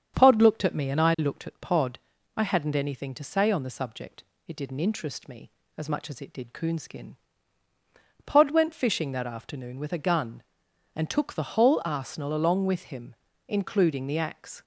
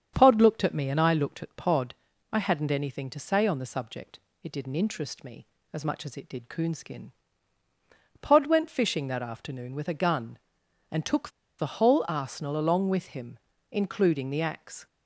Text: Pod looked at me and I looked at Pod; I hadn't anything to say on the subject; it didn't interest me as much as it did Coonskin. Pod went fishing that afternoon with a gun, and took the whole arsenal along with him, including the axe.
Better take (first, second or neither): first